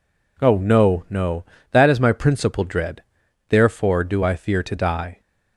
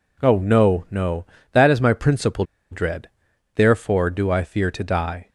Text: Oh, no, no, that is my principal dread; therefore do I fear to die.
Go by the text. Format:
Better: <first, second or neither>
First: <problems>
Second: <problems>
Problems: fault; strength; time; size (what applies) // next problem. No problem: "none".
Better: first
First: none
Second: pauses between "principal" and "dread"; slight; at 2.4 s; 0.27 s long